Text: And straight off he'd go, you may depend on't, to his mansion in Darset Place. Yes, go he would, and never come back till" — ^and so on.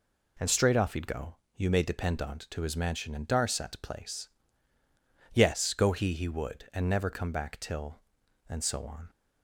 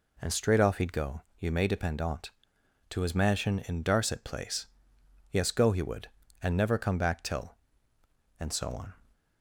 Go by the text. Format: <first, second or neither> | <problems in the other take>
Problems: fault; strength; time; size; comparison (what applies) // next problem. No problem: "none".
second | says "he" twice; at 6.1 s